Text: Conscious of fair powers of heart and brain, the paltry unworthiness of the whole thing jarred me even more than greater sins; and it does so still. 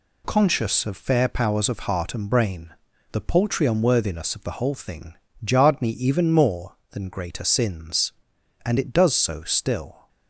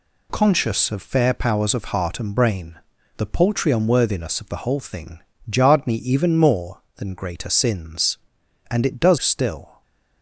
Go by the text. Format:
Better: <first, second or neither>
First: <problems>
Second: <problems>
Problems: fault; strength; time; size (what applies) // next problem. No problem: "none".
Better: first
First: pauses between "thing" and "jarred"; slight; at 5.1 s; 0.28 s long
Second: pauses between "thing" and "jarred"; slight; at 5.2 s; 0.28 s long // skips "so"; at 9.1 s